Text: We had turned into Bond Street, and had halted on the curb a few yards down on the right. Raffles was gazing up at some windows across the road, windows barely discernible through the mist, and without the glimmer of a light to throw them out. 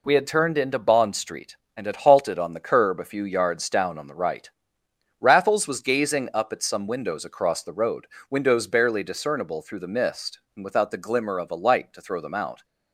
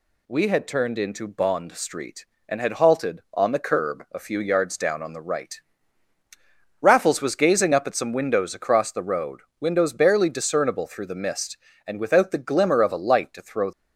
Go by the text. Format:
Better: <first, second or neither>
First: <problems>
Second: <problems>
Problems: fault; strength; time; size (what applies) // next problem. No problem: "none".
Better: first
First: none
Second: stops before "them out"; at 13.7 s